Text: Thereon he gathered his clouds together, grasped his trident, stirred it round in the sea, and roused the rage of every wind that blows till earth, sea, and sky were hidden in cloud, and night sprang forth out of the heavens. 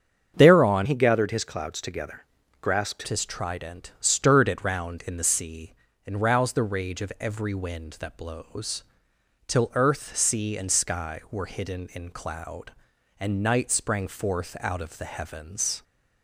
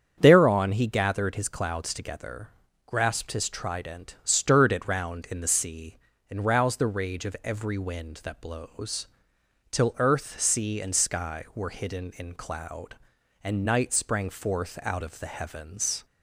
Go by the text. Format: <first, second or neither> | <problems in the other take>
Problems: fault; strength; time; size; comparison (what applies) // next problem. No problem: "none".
second | starts louder than the rest; strong; until 1.3 s; 7.5 dB; strong in the second // changes voice from "he" to "grasped"; from 0.8 to 3.0 s; 2.2 s long // pauses between "blows" and "till"; noticeable; at 8.8 s; 0.64 s long; noticeable in the second